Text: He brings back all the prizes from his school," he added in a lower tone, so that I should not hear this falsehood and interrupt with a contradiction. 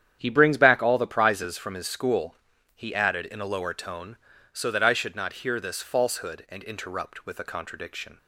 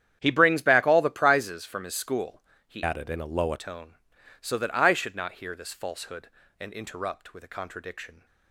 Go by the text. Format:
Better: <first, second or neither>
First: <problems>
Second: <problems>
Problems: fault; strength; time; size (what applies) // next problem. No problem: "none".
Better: first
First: starts louder than the rest; strong; until 1.2 s; 9.5 dB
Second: starts louder than the rest; strong; until 1.2 s; 10 dB // changes voice from "added" to "lower"; from 2.8 to 3.5 s; 0.7 s long